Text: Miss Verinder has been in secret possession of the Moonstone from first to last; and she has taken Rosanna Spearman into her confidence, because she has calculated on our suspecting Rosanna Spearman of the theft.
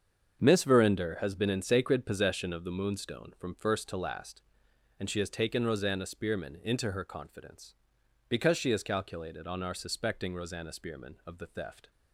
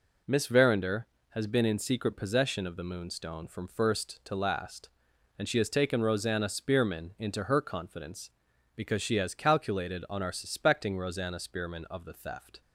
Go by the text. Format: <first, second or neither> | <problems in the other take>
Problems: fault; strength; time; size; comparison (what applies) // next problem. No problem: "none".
second | starts louder than the rest; strong; until 1.4 s; 7 dB // says "sacred" for "secret"; at 1.6 s